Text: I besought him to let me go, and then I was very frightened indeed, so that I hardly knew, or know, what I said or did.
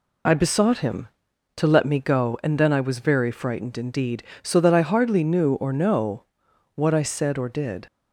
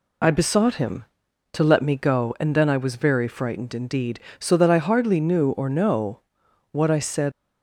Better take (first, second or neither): first